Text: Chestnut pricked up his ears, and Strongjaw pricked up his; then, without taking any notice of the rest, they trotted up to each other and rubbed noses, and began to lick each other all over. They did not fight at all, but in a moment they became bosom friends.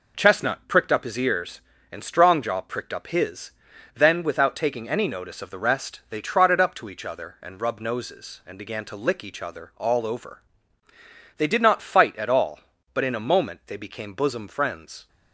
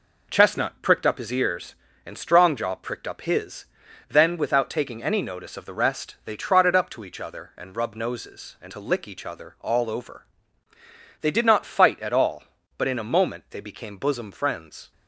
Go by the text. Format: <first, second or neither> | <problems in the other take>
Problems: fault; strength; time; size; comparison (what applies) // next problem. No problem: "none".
first | skips "began"; at 8.7 s